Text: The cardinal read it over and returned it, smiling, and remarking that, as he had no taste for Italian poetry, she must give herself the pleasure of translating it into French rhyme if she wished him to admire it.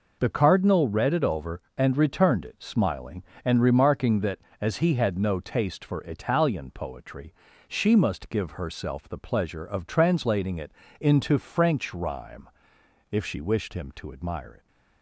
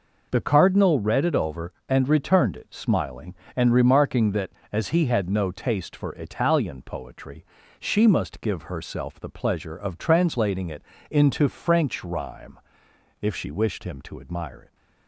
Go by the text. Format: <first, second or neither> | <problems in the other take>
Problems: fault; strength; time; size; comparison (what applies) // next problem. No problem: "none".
neither | pauses between "it" and "into"; slight; the same in both // pauses between "rhyme" and "if"; noticeable; the same in both